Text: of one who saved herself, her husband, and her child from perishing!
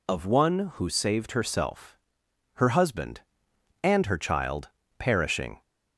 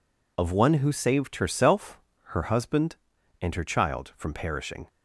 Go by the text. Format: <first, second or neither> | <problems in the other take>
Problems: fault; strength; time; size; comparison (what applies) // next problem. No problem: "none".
second | skips "from"; at 4.8 s